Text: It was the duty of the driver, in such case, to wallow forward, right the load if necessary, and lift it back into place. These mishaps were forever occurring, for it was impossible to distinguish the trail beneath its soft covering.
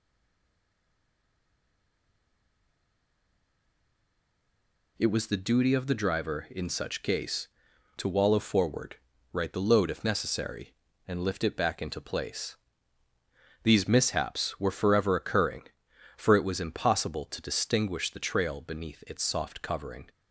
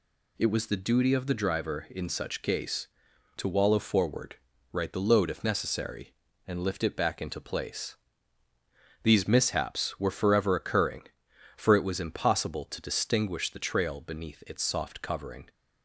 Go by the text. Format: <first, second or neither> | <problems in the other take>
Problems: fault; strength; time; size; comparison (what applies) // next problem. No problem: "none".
second | stays silent before the first word; strong; until 4.9 s; 4.9 s long